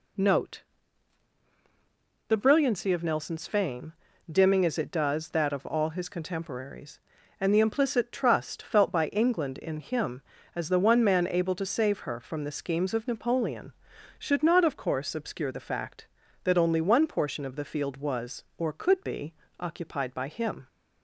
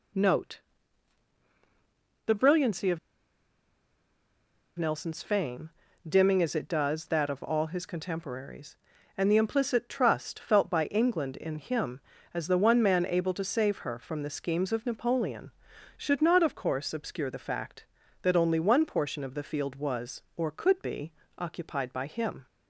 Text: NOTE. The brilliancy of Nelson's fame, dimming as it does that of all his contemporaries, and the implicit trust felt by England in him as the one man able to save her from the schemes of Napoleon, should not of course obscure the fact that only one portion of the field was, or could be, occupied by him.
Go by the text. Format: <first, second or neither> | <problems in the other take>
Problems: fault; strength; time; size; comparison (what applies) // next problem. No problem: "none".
first | pauses between "of" and "Nelson's"; strong; at 2.9 s; 1.8 s long